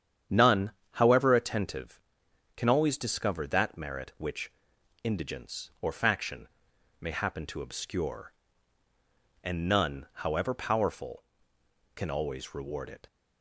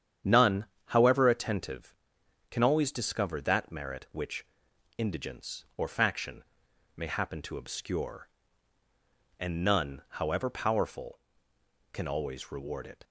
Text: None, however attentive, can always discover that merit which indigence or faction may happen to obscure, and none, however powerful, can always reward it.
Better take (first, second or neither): neither